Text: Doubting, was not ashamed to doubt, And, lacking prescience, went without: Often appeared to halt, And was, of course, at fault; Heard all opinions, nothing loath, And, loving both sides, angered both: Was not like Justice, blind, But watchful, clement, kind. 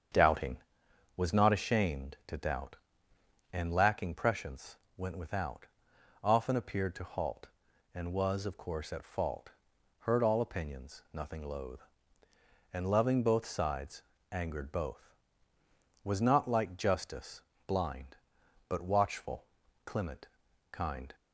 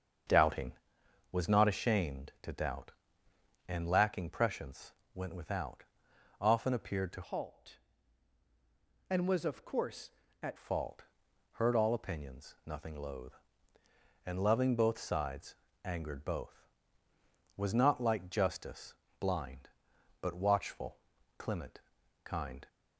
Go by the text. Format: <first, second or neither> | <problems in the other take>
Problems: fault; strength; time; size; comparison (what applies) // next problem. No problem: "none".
first | starts louder than the rest; strong; until 1.8 s; 7 dB; strong in the first // changes voice from "halt" to "at"; from 7.2 to 10.5 s; 3.3 s long